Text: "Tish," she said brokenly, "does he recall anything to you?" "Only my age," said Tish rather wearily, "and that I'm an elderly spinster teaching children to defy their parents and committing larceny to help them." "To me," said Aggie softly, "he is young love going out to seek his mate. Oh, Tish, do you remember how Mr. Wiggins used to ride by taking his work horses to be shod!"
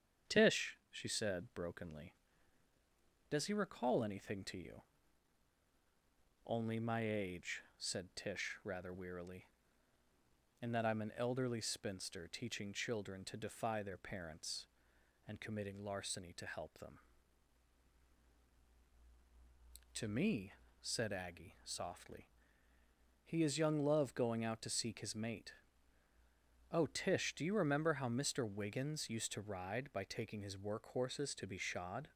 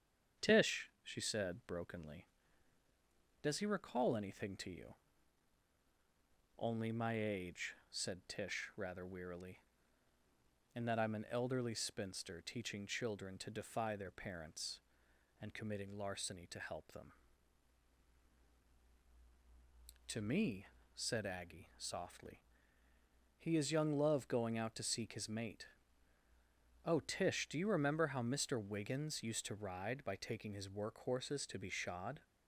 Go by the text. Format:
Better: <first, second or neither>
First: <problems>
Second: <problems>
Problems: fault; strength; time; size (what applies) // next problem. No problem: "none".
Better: neither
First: starts louder than the rest; strong; until 1.4 s; 8 dB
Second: starts louder than the rest; strong; until 1.5 s; 8 dB